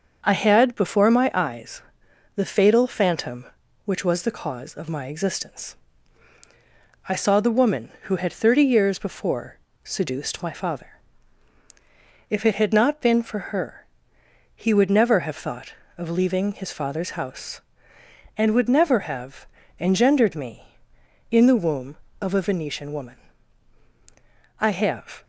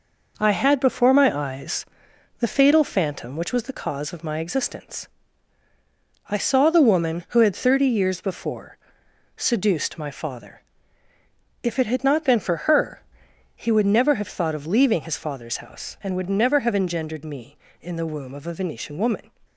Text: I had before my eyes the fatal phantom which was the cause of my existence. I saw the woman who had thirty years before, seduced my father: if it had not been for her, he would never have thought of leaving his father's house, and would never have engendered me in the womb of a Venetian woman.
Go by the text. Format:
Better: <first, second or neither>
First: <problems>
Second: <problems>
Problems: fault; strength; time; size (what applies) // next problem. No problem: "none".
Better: second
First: starts louder than the rest; until 1.2 s; 6.5 dB // pauses between "eyes" and "the"; noticeable; at 1.8 s; 0.54 s long // pauses between "have" and "engendered"; slight; at 19.4 s; 0.32 s long // goes on to say "I have"; noticeable; from 24.5 s on; 0.64 s long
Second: pauses between "eyes" and "the"; noticeable; at 1.8 s; 0.54 s long